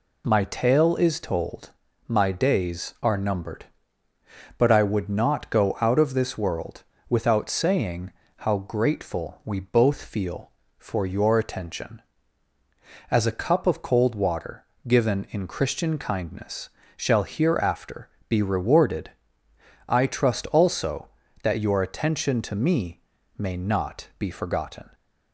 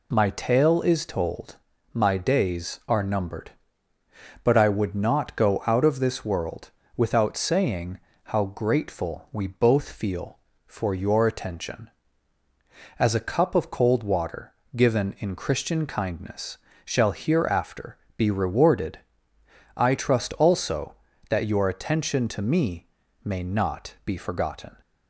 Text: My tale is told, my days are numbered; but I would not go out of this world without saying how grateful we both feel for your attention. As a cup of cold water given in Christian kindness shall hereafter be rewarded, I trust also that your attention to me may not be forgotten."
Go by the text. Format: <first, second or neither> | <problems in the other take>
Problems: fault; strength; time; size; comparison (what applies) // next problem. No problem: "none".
neither | pauses between "world" and "without"; slight; the same in both // pauses between "saying" and "how"; slight; the same in both // pauses between "water" and "given"; slight; the same in both // pauses between "kindness" and "shall"; slight; the same in both // pauses between "hereafter" and "be"; slight; the same in both // pauses between "me" and "may"; slight; the same in both